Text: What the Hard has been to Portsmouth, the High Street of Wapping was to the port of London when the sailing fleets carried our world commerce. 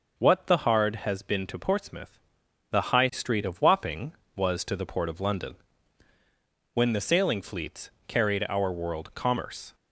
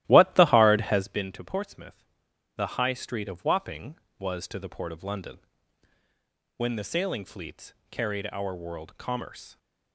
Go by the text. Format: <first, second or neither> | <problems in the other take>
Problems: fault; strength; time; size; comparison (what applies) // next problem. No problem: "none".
first | starts louder than the rest; strong; until 1.3 s; 15 dB // pauses between "London" and "when"; at 5.3 s; 1.1 s long; also in the first // pauses between "fleets" and "carried"; slight; at 7.7 s; 0.16 s long; slight in the first